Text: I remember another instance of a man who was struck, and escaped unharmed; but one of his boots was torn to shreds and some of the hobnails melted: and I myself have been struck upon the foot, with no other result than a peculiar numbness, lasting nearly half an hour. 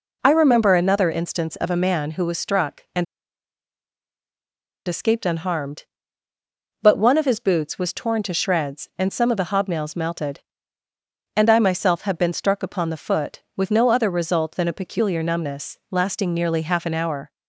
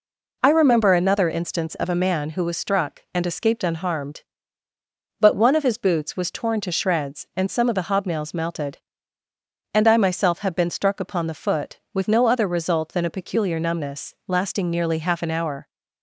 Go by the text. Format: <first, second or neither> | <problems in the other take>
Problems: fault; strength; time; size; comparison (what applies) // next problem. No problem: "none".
second | pauses between "and" and "escaped"; strong; at 3.0 s; 1.8 s long